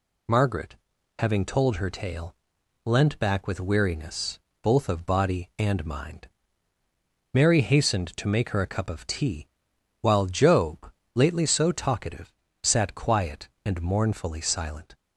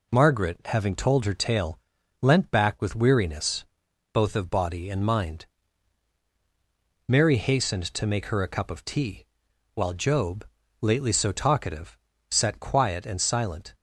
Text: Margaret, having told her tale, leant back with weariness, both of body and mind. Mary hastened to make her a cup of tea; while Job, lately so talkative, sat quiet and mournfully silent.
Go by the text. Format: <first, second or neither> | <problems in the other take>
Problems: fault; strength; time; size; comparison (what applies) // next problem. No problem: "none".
first | skips "mournfully"; at 13.2 s